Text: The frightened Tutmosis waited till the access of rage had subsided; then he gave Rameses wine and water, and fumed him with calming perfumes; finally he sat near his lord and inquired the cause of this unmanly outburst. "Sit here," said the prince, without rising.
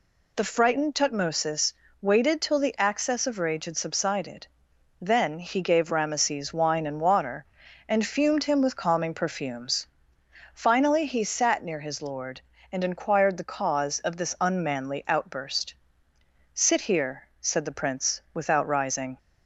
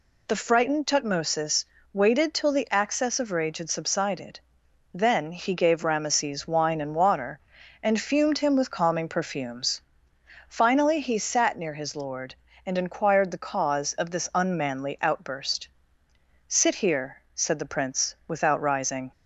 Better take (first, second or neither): neither